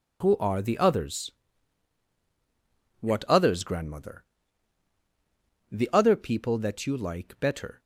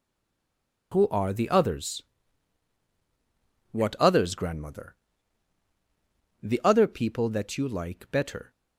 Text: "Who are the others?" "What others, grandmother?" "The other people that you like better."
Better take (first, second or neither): first